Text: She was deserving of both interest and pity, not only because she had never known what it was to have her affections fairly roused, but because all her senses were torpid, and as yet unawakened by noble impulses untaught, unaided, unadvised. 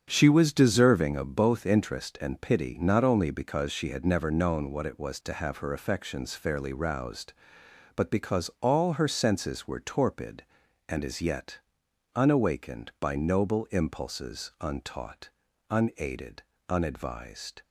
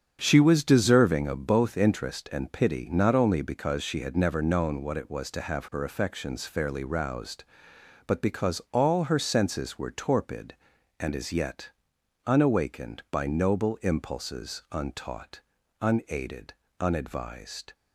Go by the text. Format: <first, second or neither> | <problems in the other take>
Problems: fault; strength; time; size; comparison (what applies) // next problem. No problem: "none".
neither | starts louder than the rest; strong; the same in both // pauses between "yet" and "unawakened"; noticeable; the same in both